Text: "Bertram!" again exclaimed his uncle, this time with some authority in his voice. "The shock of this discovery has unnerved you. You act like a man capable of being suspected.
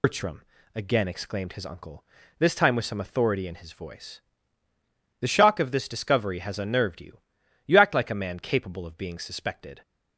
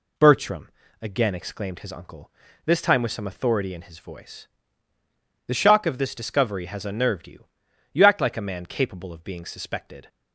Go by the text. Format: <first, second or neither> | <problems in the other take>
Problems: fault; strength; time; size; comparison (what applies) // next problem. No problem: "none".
second | loses the start of "Bertram"; at 0.0 s; 125 ms